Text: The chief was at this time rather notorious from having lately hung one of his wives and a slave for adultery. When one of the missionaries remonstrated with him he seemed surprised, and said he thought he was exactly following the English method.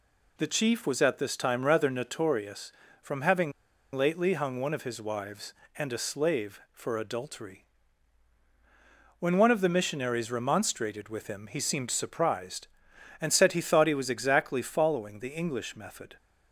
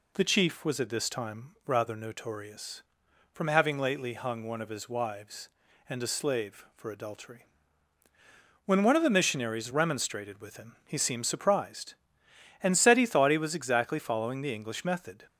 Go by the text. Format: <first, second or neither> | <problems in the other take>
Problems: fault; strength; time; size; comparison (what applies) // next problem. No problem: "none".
second | pauses between "having" and "lately"; at 3.5 s; 0.43 s long